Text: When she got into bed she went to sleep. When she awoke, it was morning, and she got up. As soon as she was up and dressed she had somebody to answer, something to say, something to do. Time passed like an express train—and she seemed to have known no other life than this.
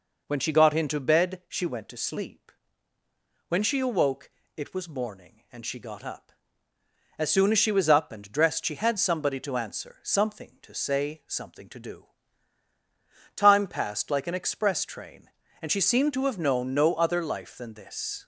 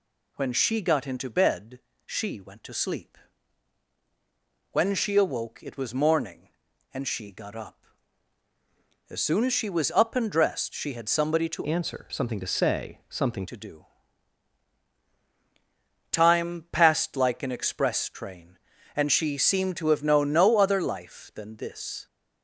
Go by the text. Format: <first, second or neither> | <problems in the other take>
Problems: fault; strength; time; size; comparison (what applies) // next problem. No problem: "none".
first | pauses between "bed" and "she"; slight; at 1.7 s; 0.26 s long // changes voice from "answer" to "something"; from 11.6 to 13.4 s; 1.8 s long